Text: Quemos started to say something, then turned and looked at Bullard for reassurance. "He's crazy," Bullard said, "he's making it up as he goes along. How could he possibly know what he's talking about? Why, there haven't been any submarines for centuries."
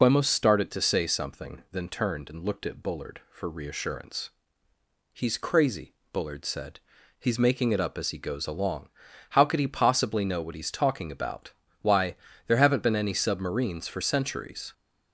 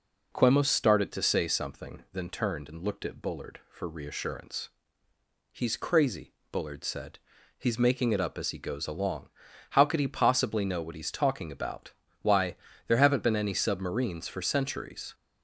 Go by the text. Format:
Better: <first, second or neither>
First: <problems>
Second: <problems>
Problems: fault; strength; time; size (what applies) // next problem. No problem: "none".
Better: second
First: loses the start of "Quemos"; at 0.0 s; 75 ms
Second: none